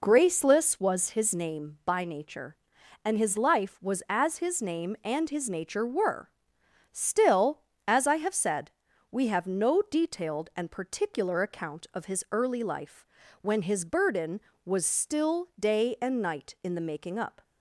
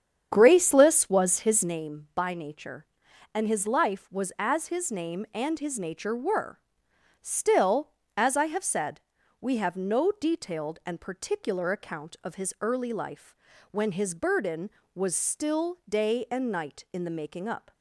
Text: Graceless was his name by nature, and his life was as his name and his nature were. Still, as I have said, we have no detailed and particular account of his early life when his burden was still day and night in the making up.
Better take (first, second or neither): first